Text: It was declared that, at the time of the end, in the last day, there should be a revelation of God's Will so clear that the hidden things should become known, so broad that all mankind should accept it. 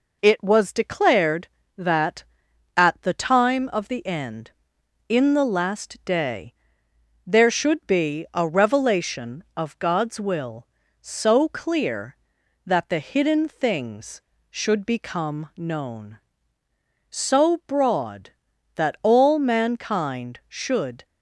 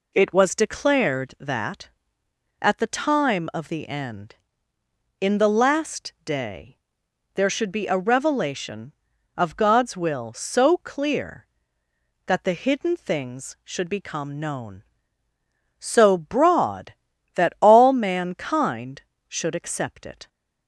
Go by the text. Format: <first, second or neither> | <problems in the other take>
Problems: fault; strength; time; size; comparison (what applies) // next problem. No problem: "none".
second | stops before "accept it"; at 21.0 s